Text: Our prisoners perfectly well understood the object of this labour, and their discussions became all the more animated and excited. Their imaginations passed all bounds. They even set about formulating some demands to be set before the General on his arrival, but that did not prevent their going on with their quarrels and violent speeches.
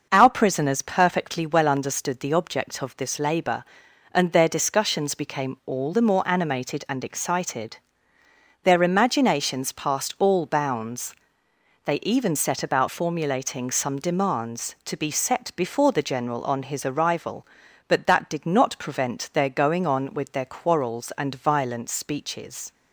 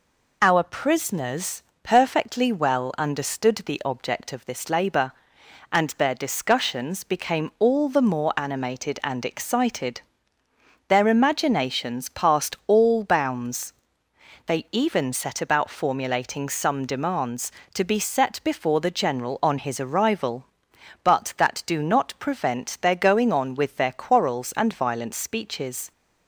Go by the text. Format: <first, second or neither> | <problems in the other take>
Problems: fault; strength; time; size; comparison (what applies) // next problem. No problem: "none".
first | pauses between "prisoners" and "perfectly"; slight; at 1.6 s; 0.20 s long // says "do" for "did"; at 21.6 s